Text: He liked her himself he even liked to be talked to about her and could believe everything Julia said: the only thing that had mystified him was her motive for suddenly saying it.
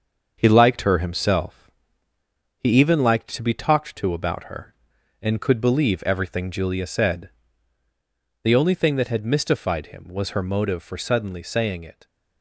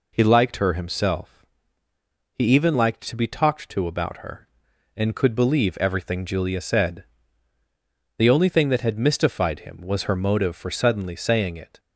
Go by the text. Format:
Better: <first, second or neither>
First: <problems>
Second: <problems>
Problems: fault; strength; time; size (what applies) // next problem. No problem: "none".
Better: second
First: gets quieter; noticeable; throughout; 4.5 dB // pauses between "himself" and "he"; noticeable; at 1.6 s; 0.90 s long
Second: pauses between "himself" and "he"; noticeable; at 1.4 s; 0.90 s long